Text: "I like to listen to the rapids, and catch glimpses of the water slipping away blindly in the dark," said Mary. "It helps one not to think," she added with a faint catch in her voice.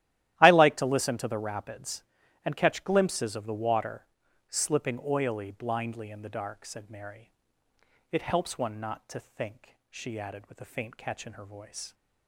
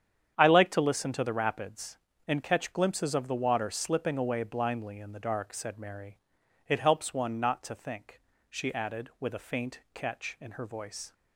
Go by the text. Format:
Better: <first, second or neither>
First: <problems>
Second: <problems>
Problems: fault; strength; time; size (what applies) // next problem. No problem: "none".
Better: second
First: starts louder than the rest; strong; until 1.4 s; 13.5 dB // pauses between "water" and "slipping"; noticeable; at 4.0 s; 0.46 s long // says "oily" for "away"; at 5.0 s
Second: starts louder than the rest; strong; until 1.3 s; 8.5 dB